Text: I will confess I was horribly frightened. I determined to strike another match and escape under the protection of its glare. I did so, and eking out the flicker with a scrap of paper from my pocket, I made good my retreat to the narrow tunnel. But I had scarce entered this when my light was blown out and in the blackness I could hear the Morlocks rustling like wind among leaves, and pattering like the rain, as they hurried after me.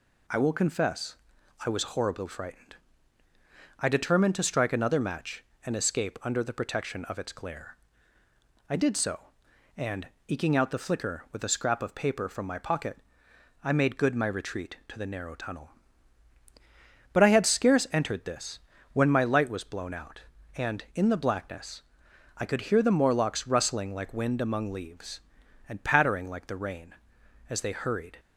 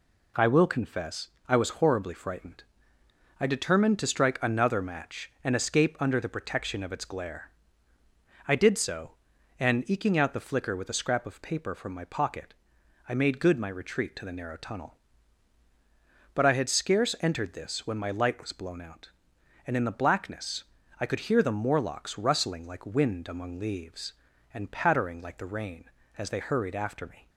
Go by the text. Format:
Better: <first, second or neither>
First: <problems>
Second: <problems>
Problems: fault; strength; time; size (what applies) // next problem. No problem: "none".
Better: second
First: pauses between "confess" and "I"; noticeable; at 1.1 s; 0.50 s long // pauses between "and" and "eking"; slight; at 10.0 s; 0.18 s long // pauses between "this" and "when"; slight; at 18.5 s; 0.32 s long // pauses between "blackness" and "I"; noticeable; at 21.8 s; 0.54 s long // stops before "after me"; at 28.1 s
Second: pauses between "confess" and "I"; slight; at 1.2 s; 0.18 s long // pauses between "blackness" and "I"; slight; at 20.6 s; 0.36 s long